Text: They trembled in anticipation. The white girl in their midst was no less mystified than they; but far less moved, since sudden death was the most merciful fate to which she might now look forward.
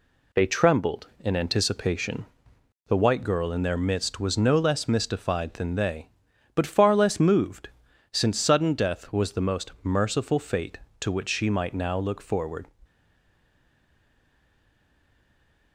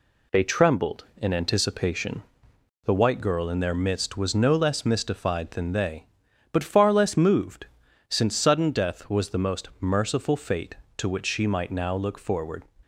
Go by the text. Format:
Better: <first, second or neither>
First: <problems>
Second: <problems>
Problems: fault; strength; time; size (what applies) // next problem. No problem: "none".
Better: second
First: stays silent after the last word; strong; from 12.8 s on; 2.9 s long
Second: none